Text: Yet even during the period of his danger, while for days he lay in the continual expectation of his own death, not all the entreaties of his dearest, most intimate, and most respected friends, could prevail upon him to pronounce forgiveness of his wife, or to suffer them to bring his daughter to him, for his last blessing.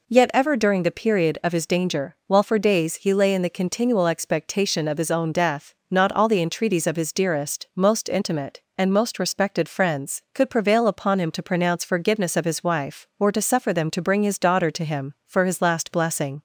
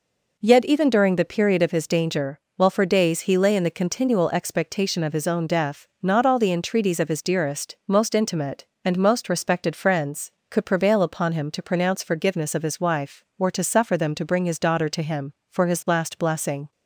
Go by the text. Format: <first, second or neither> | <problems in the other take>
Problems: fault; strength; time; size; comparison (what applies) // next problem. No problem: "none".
second | says "ever" for "even"; at 0.3 s